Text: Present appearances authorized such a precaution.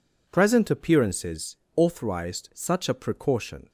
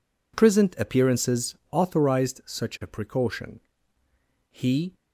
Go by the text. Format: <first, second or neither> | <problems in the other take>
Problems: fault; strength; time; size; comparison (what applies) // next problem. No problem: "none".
first | pauses between "appearances" and "authorized"; slight; at 1.5 s; 0.16 s long; slight in the first // goes on to say "He"; slight; from 4.5 s on; 0.42 s long